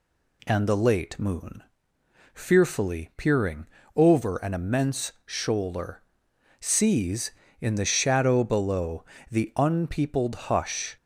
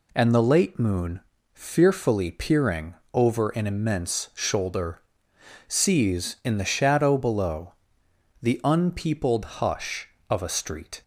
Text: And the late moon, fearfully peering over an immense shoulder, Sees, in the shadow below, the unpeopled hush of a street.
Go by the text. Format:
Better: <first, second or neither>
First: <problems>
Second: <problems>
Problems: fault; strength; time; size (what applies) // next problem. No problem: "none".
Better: second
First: pauses between "peering" and "over"; slight; at 3.6 s; 0.28 s long // stops before "of a street"; at 10.9 s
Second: pauses between "peering" and "over"; slight; at 2.9 s; 0.20 s long